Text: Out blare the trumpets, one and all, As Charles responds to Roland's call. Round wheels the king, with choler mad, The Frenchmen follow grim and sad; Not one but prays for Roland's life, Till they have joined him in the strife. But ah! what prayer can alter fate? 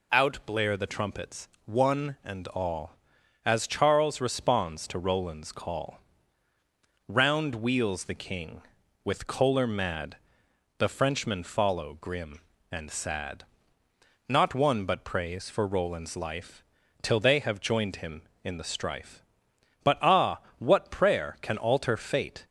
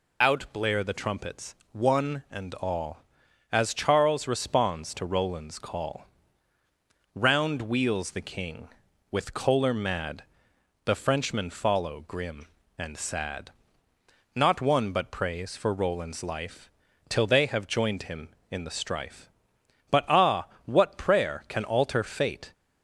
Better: first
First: none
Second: loses the start of "Out"; at 0.2 s; 20 ms

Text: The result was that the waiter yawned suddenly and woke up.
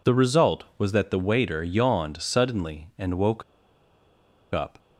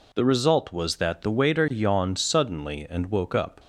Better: second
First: pauses between "woke" and "up"; at 3.4 s; 1.0 s long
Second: none

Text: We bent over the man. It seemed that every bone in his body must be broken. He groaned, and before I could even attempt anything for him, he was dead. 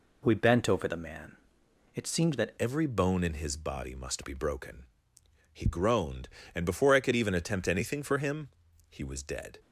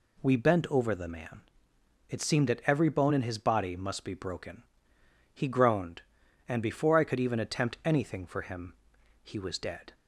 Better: second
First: changes voice at "every"; from 2.5 s on; 7.0 s long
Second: none

